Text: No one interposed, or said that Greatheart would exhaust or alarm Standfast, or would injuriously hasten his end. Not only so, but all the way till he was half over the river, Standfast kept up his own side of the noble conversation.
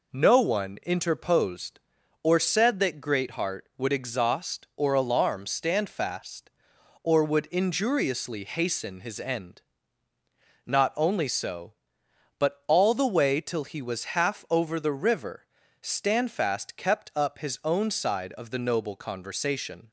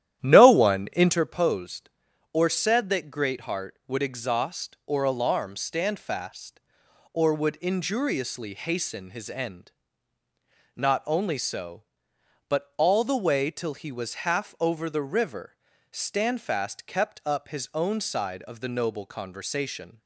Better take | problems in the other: first | starts louder than the rest; strong; until 1.3 s; 11.5 dB

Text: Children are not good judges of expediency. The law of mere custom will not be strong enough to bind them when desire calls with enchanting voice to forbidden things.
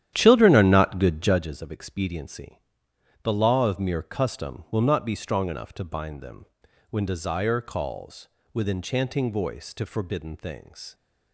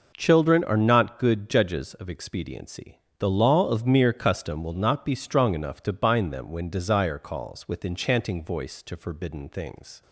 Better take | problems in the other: second | starts louder than the rest; strong; until 1.4 s; 11 dB // pauses between "them" and "when"; at 6.4 s; 0.44 s long

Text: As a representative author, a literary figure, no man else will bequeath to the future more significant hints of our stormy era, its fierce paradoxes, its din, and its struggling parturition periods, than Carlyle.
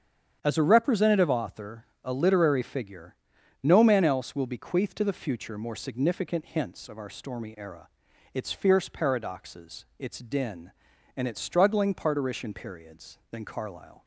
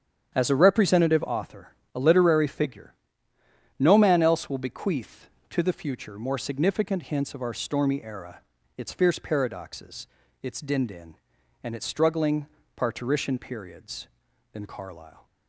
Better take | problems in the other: first | starts louder than the rest; strong; until 1.3 s; 9 dB; strong in the first // says "din" twice; at 10.8 s // pauses between "struggling" and "parturition"; slight; at 12.4 s; 0.30 s long

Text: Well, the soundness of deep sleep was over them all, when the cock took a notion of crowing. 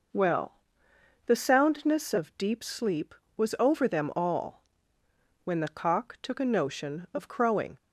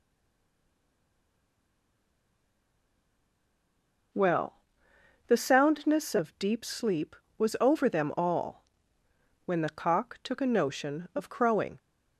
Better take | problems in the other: first | stays silent before the first word; strong; until 4.1 s; 4.1 s long

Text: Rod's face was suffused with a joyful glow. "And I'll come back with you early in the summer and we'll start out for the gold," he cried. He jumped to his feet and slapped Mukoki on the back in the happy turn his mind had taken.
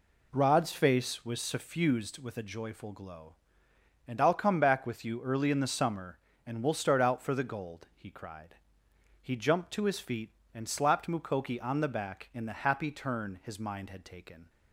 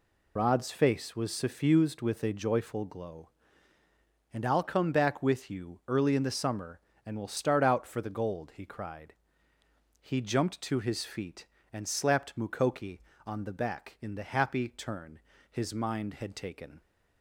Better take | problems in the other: first | loses the start of "Rod's"; at 0.3 s; 40 ms // pauses between "turn" and "his"; slight; at 15.1 s; 0.32 s long

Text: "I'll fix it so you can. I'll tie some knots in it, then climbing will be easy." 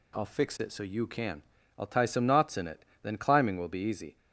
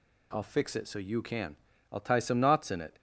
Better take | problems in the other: first | stops before "then climbing will be easy"; at 2.9 s

